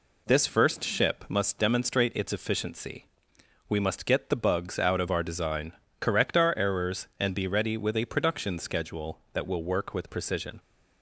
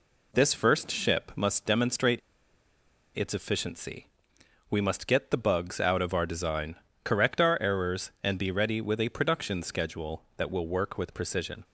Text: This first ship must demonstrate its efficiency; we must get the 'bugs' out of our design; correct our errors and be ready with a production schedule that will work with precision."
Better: first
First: none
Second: pauses between "demonstrate" and "its"; noticeable; at 2.2 s; 0.97 s long

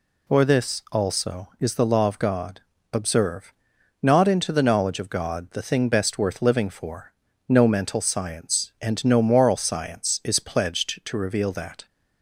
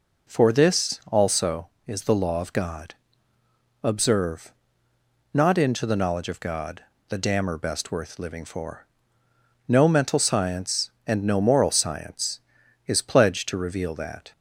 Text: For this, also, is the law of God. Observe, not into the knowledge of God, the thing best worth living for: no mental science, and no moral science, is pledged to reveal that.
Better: first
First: none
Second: says "dammer" for "thing"; at 7.1 s

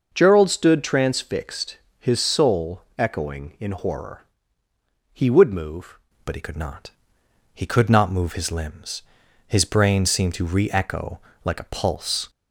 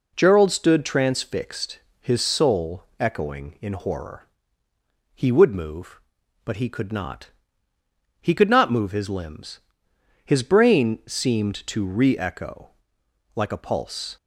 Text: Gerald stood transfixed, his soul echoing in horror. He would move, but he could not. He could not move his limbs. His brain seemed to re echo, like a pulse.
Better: second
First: pauses between "soul" and "echoing"; slight; at 2.8 s; 0.16 s long // changes voice at "but"; from 6.2 s on; 6.0 s long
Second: pauses between "soul" and "echoing"; slight; at 2.8 s; 0.16 s long

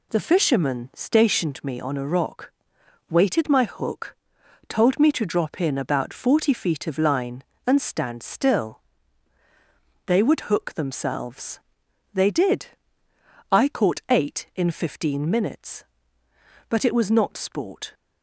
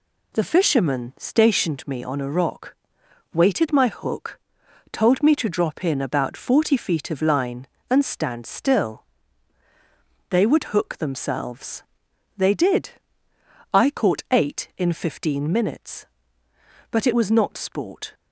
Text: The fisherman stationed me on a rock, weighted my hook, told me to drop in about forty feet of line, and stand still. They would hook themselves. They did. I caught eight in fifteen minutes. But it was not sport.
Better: neither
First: none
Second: none

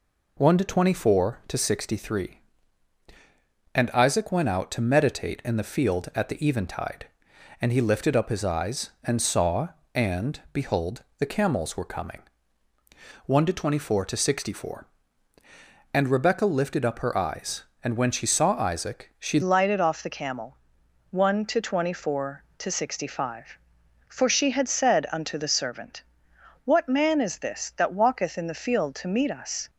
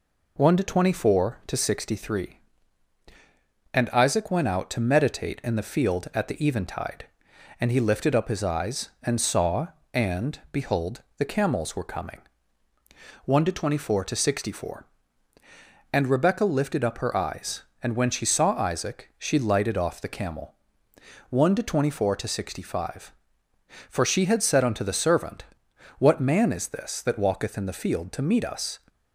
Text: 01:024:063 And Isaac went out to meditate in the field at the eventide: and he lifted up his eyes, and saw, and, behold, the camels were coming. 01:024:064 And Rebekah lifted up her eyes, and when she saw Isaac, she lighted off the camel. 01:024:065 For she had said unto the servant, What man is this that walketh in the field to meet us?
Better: second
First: changes voice at "lighted"; from 19.4 s on; 10.2 s long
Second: none

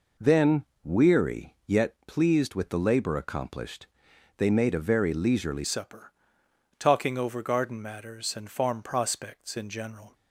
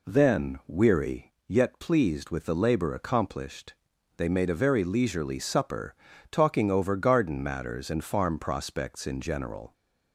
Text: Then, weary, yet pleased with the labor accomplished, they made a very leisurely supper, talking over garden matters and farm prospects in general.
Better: second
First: changes voice at "supper"; from 5.6 s on; 4.5 s long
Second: none

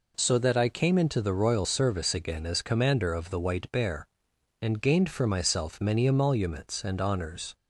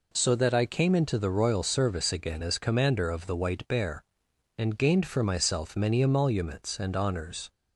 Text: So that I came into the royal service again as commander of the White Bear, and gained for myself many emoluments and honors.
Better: neither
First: none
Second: none

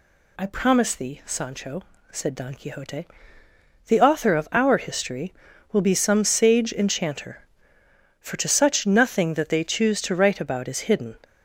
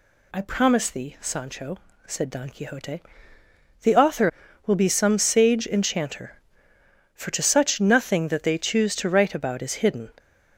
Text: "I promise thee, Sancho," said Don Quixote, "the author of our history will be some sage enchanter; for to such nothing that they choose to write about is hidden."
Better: first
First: none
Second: skips "of our history"; at 4.4 s

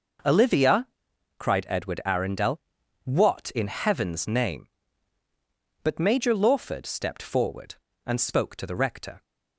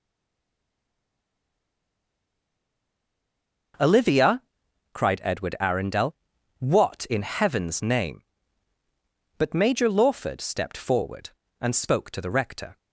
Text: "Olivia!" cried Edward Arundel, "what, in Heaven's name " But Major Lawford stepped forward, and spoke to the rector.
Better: first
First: starts louder than the rest; noticeable; until 1.7 s; 6 dB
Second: stays silent before the first word; strong; until 3.7 s; 3.7 s long // starts louder than the rest; noticeable; until 5.3 s; 6 dB

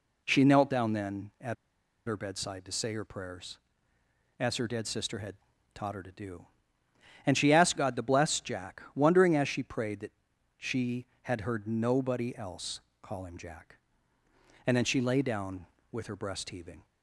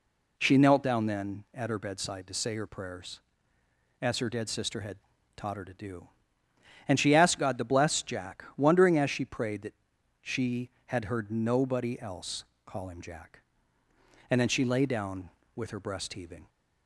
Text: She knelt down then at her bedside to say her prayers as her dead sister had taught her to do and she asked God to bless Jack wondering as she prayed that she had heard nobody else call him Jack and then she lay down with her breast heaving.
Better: second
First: pauses between "at" and "her"; noticeable; at 1.5 s; 0.51 s long // pauses between "had" and "taught"; at 5.3 s; 0.38 s long // pauses between "that" and "she"; at 10.1 s; 0.44 s long // pauses between "else" and "call"; slight; at 12.7 s; 0.22 s long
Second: pauses between "had" and "taught"; at 4.9 s; 0.38 s long // pauses between "that" and "she"; at 9.7 s; 0.45 s long // pauses between "else" and "call"; slight; at 12.4 s; 0.22 s long

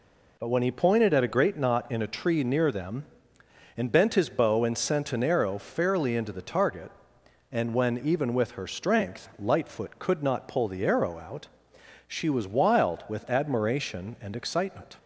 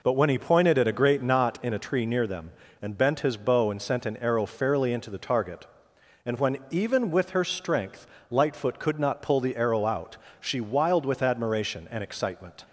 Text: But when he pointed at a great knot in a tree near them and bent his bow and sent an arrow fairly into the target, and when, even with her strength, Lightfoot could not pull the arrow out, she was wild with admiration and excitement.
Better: first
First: none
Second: skips "was"; at 10.6 s

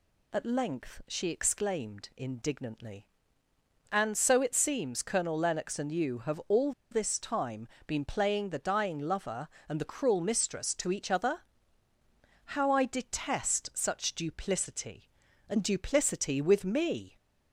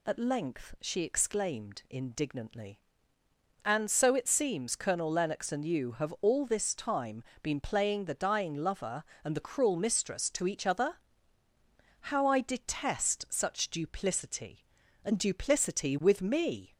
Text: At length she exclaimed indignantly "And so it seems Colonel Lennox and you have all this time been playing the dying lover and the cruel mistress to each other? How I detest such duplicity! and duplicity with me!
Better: second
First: pauses between "all" and "this"; slight; at 6.7 s; 0.20 s long // pauses between "time" and "been"; slight; at 7.6 s; 0.22 s long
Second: pauses between "time" and "been"; slight; at 7.2 s; 0.22 s long

